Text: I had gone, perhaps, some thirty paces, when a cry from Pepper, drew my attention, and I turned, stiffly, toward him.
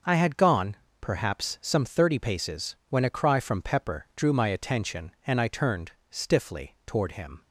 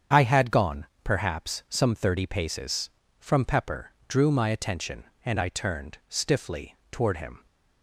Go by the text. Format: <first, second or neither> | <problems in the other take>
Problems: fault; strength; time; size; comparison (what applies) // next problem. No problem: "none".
first | starts louder than the rest; strong; until 1.3 s; 7.5 dB // skips "when a cry"; at 3.0 s